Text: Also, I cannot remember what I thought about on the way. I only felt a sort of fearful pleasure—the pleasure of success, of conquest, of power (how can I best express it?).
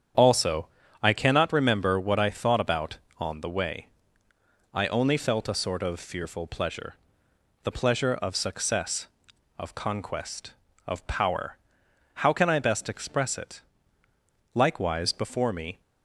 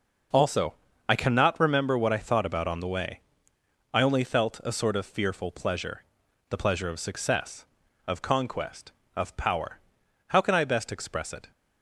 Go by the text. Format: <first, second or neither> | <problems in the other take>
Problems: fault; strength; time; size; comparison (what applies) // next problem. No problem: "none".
second | starts louder than the rest; strong; until 1.5 s; 8.5 dB // goes on to say "Likewise before me"; noticeable; from 14.5 s on; 1.2 s long